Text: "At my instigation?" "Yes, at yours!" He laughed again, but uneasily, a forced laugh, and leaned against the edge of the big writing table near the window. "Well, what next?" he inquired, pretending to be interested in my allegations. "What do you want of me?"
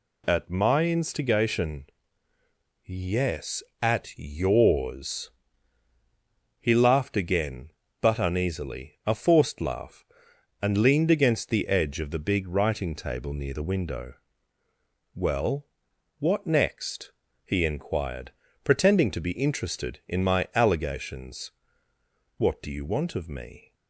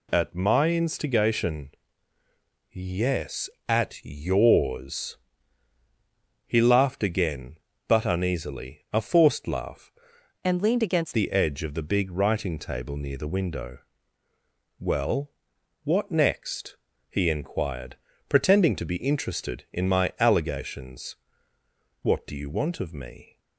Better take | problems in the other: first | changes voice from "and" to "against"; from 10.4 to 11.1 s; 0.7 s long

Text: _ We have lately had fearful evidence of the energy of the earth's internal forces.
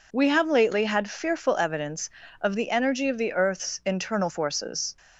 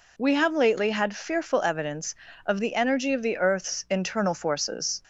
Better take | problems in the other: second | gets quieter; throughout; 6.5 dB

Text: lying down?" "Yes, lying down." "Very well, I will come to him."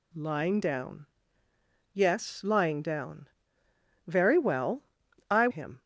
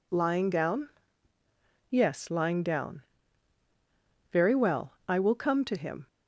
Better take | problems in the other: second | skips "will come to"; at 5.4 s

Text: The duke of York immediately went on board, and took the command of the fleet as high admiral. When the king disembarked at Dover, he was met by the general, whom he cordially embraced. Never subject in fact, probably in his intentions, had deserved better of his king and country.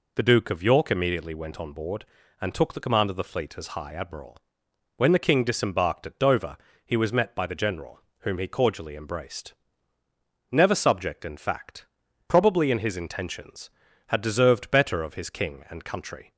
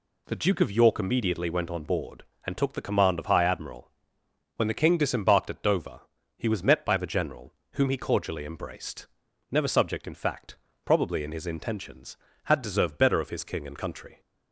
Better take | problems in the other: first | skips "the fleet as"; at 3.2 s

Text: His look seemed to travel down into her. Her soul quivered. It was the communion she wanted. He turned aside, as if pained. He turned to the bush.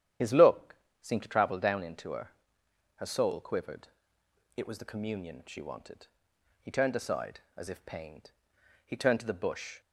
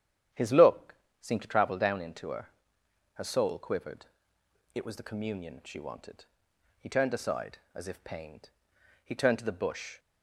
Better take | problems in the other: second | loses the start of "His"; at 0.2 s; 50 ms // starts louder than the rest; strong; until 1.4 s; 10 dB; strong in the second // pauses between "look" and "seemed"; slight; at 0.7 s; 0.26 s long; slight in the second

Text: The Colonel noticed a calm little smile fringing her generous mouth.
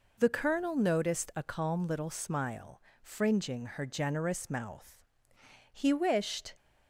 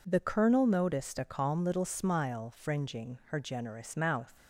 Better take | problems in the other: second | pauses between "smile" and "fringing"; slight; at 2.8 s; 0.22 s long // goes on to say "He wished"; noticeable; from 5.7 s on; 0.82 s long

